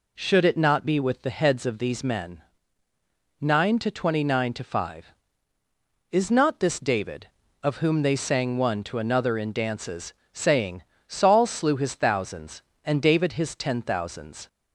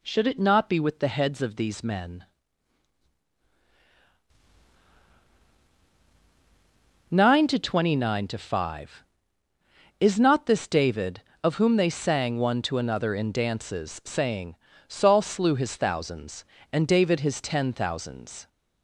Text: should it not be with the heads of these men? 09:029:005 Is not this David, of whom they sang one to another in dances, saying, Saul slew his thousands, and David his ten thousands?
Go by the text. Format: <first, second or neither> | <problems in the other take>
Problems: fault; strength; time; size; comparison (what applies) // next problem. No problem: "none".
neither | none